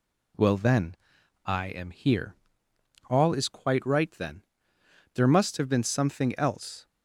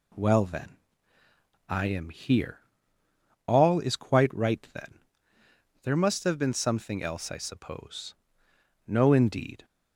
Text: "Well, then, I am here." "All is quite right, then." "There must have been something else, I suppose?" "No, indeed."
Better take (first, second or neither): second